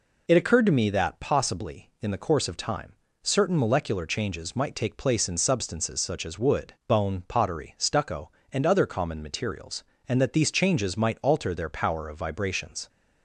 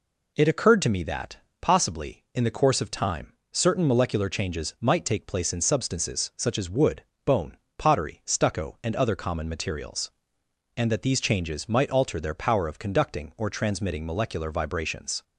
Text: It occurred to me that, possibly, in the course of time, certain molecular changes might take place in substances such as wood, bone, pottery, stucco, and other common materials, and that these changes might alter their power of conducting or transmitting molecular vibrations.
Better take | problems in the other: second | skips "conducting or transmitting molecular"; at 12.1 s

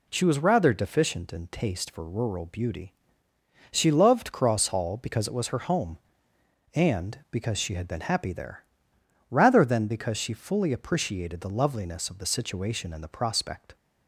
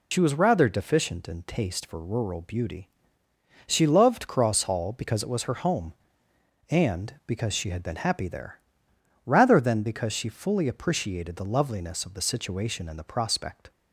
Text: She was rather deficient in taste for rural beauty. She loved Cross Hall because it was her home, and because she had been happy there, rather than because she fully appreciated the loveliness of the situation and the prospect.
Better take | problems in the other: first | loses the start of "She"; at 0.1 s; 60 ms

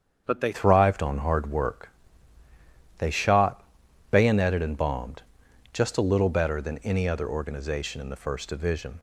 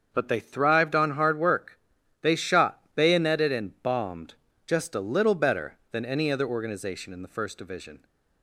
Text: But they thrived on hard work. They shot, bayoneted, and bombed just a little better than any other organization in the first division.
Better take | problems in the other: second | starts louder than the rest; strong; until 1.2 s; 7.5 dB; also in the second // changes voice at "thrived"; from 0.5 s on; 8.4 s long // pauses between "bombed" and "just"; noticeable; at 5.2 s; 0.52 s long; slight in the second

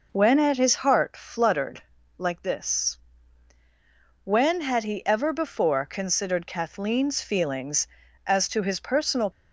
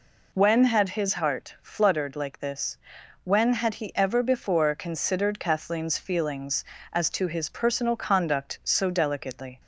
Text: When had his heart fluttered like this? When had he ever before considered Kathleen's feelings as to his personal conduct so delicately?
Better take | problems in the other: second | pauses between "fluttered" and "like"; slight; at 1.8 s; 0.34 s long // stops before "conduct so delicately"; at 9.3 s

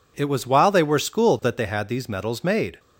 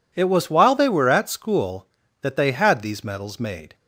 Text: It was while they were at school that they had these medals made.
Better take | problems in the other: second | skips "at"; at 0.9 s

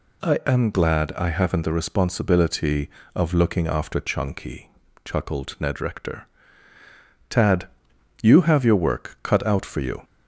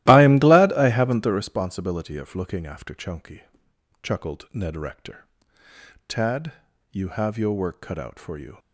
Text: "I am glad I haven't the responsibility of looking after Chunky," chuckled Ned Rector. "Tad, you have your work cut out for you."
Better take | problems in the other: first | starts louder than the rest; strong; until 1.6 s; 16 dB

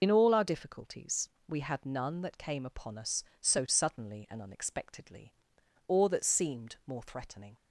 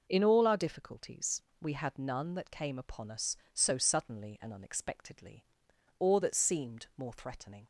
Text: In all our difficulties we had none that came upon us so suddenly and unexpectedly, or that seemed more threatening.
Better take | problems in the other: second | loses the start of "In"; at 0.0 s; 60 ms // pauses between "difficulties" and "we"; slight; at 1.2 s; 0.20 s long; slight in the second

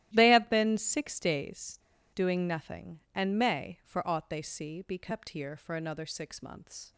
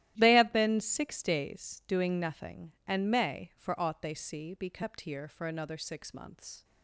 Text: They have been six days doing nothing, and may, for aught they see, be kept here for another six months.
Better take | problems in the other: second | starts louder than the rest; strong; until 1.1 s; 13.5 dB; strong in the second // pauses between "days" and "doing"; at 1.7 s; 0.38 s long

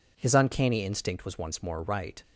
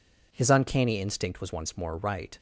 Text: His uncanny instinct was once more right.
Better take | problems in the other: neither | none

